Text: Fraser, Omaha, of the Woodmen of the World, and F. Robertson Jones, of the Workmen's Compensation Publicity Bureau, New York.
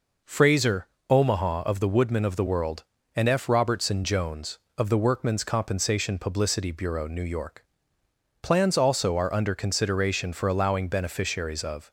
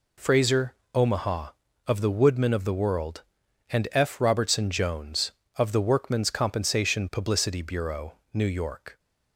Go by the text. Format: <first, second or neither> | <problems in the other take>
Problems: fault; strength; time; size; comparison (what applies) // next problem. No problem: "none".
second | goes on to say "Plans also are under consideration for allowing beneficiaries of"; strong; from 8.4 s on; 3.4 s long